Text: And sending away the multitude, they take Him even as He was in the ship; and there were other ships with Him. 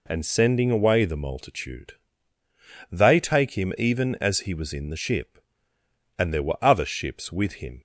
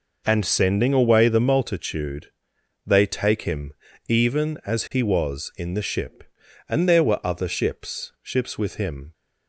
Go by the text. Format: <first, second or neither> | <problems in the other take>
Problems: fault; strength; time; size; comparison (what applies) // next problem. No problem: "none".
first | pauses between "Him" and "even"; slight; at 3.7 s; 0.34 s long // says "ships" twice; at 8.2 s